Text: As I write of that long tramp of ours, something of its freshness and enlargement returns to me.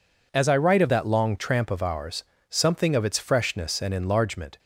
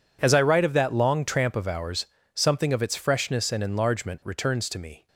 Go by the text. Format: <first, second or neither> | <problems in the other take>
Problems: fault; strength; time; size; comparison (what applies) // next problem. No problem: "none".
second | stops before "returns to me"; at 4.5 s